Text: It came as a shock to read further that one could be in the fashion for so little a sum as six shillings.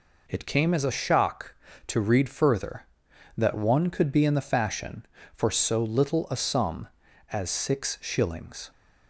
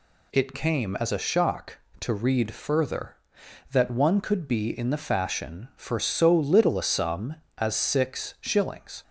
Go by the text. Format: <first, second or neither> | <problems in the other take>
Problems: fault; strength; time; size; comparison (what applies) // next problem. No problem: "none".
neither | none